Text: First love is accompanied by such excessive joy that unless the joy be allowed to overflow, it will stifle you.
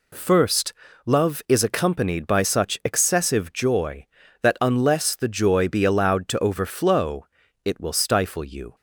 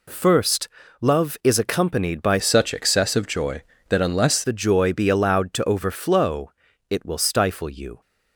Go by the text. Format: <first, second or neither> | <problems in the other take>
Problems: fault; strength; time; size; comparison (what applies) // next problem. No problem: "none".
first | pauses between "First" and "love"; slight; at 0.6 s; 0.32 s long; slight in the first // changes voice from "such" to "unless"; from 2.3 to 4.4 s; 2.1 s long